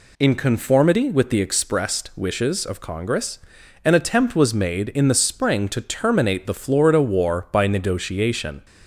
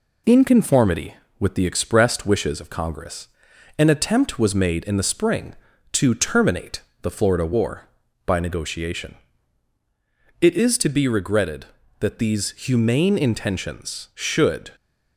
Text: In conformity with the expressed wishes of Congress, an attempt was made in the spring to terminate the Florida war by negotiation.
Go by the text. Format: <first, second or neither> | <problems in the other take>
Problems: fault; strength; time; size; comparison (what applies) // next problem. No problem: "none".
first | pauses between "terminate" and "the"; slight; at 6.8 s; 0.22 s long // goes on to say "It is to be regretted that these humane intentions should"; strong; from 10.4 s on; 4.3 s long